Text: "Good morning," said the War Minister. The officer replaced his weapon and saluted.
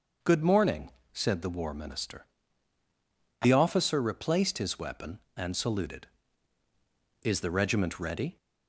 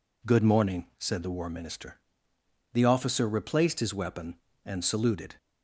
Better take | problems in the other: second | starts louder than the rest; noticeable; until 1.4 s; 6 dB // goes on to say "Is the regiment ready"; noticeable; from 7.2 s on; 1.1 s long

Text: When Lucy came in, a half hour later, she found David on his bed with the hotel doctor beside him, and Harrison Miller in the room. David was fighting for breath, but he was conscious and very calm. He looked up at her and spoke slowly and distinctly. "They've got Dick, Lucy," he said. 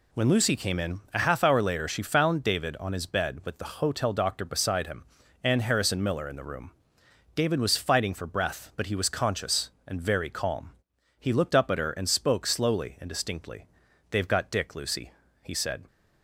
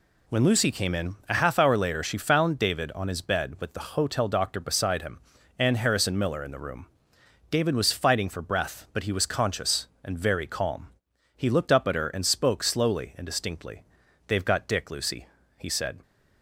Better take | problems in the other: neither | none

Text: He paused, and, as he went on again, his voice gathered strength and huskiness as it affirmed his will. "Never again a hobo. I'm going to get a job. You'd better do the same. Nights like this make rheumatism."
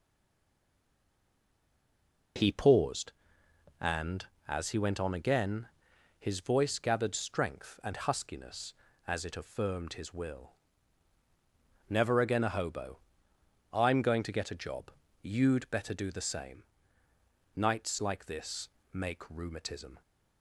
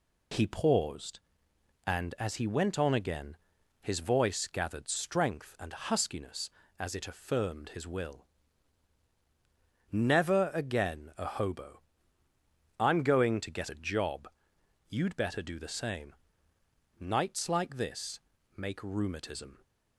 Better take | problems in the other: second | stays silent before the first word; until 2.3 s; 2.3 s long // pauses between "this" and "make"; slight; at 18.6 s; 0.24 s long; slight in the second

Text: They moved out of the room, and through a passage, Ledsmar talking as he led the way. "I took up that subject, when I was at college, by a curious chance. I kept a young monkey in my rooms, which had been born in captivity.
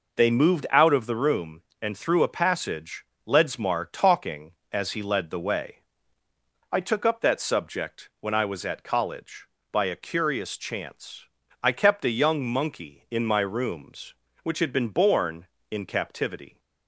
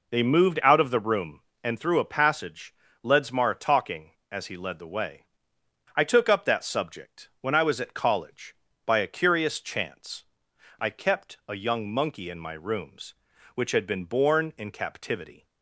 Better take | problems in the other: neither | none

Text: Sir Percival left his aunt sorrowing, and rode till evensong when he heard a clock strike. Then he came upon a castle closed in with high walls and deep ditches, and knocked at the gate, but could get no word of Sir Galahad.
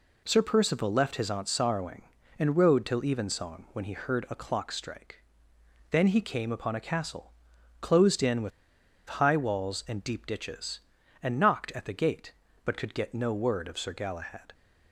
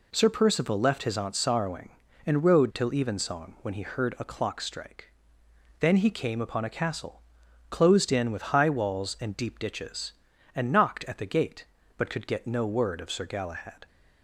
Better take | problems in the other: second | pauses between "castle" and "closed"; noticeable; at 7.3 s; 0.50 s long; noticeable in the second // pauses between "with" and "high"; noticeable; at 8.5 s; 0.69 s long

